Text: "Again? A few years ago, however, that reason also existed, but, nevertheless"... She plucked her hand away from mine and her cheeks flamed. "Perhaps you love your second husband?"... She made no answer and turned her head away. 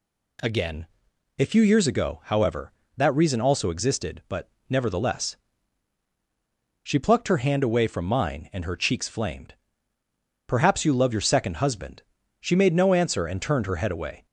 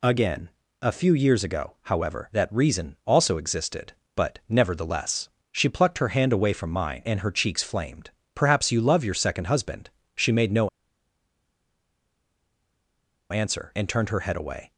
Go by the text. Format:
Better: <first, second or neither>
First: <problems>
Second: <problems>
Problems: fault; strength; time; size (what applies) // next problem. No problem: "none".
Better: first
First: none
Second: pauses between "no" and "answer"; strong; at 10.6 s; 2.6 s long